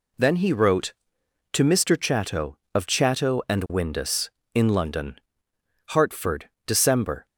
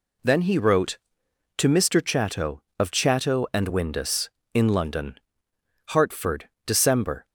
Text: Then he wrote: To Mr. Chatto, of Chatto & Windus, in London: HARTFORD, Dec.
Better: neither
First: none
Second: none

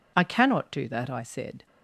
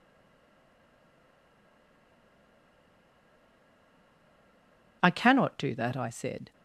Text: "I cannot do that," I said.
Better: first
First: none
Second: stays silent before the first word; strong; until 5.0 s; 5.0 s long

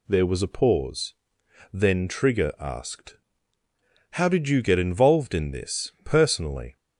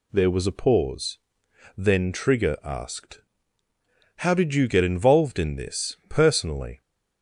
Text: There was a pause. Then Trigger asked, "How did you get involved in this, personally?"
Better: neither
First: none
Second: none

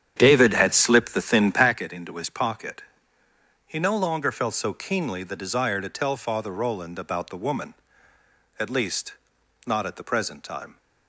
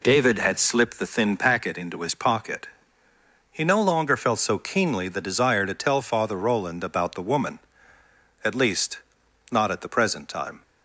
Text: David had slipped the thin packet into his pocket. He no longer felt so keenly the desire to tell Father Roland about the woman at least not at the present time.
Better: second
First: starts louder than the rest; strong; until 1.8 s; 9.5 dB // pauses between "least" and "not"; noticeable; at 9.1 s; 0.54 s long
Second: pauses between "least" and "not"; noticeable; at 8.9 s; 0.54 s long

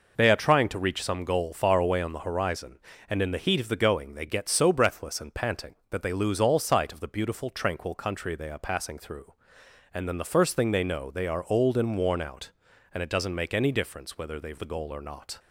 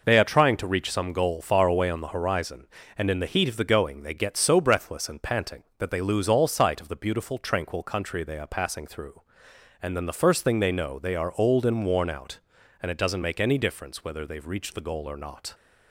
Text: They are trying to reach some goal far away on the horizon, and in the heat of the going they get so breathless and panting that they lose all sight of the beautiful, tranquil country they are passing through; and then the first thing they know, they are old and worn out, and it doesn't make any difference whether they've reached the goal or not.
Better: second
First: skips "reached"; at 14.5 s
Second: none

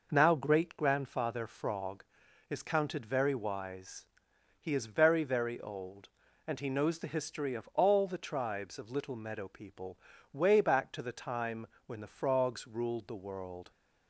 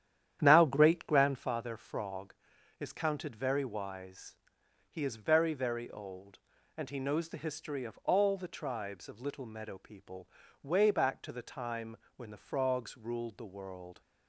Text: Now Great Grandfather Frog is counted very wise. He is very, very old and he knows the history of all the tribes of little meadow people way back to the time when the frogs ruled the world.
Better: first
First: pauses between "people" and "way"; slight; at 9.9 s; 0.36 s long // pauses between "time" and "when"; slight; at 11.6 s; 0.20 s long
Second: starts louder than the rest; strong; until 1.6 s; 10 dB // pauses between "people" and "way"; slight; at 10.2 s; 0.36 s long // pauses between "time" and "when"; slight; at 11.9 s; 0.20 s long

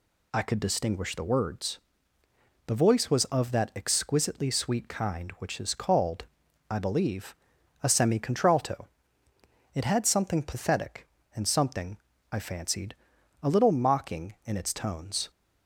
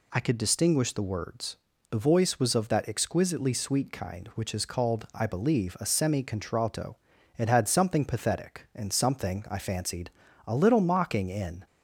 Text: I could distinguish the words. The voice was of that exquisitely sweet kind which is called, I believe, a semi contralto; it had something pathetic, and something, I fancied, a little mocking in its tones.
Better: first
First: none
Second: stops before "its tones"; at 11.6 s

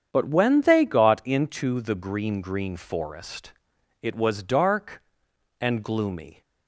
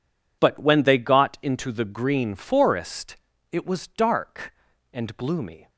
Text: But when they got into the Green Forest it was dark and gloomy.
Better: second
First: starts louder than the rest; strong; until 1.1 s; 8 dB // says "Green" twice; at 2.4 s // pauses between "Forest" and "it"; noticeable; at 3.5 s; 0.50 s long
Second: pauses between "Forest" and "it"; slight; at 3.1 s; 0.36 s long

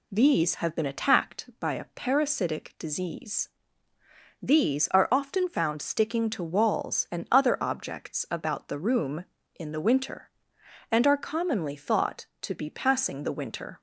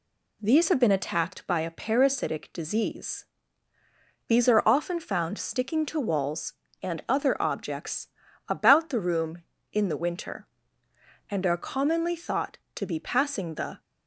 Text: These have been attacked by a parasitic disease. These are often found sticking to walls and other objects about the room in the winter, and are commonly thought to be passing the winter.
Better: first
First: none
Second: pauses between "objects" and "about"; at 8.0 s; 0.40 s long // stops before "winter"; at 13.7 s

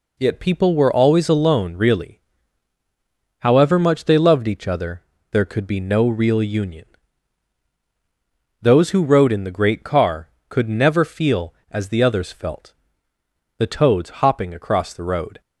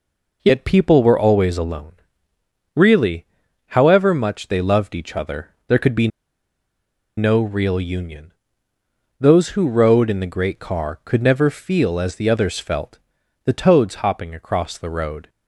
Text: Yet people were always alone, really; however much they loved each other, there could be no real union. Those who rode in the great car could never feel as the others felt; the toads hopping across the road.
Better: first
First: none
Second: pauses between "be" and "no"; at 6.0 s; 1.0 s long

